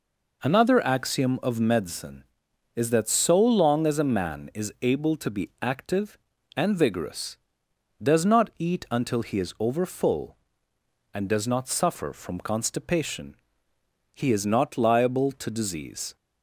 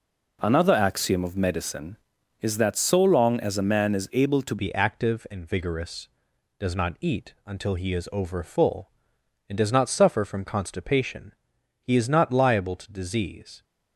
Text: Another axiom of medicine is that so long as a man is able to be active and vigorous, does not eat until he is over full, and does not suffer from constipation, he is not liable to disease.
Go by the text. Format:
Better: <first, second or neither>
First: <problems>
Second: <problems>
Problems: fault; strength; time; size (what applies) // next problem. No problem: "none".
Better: first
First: none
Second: changes voice at "be"; from 4.5 s on; 9.1 s long